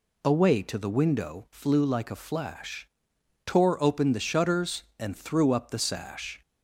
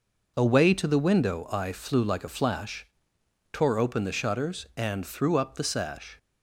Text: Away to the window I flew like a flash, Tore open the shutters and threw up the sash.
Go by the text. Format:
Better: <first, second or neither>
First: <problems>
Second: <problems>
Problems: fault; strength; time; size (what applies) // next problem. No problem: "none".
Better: second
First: skips "I"; at 1.4 s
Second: none